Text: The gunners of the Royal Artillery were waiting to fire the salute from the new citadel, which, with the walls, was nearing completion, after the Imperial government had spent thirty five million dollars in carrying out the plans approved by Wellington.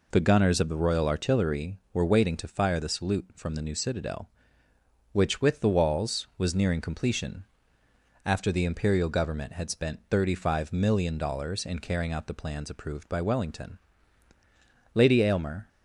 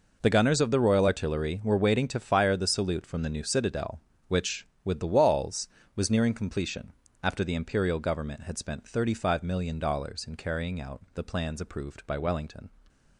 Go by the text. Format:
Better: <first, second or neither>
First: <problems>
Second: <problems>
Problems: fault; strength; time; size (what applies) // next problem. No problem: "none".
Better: second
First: goes on to say "Lady Aylmer"; noticeable; from 14.9 s on; 0.74 s long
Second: none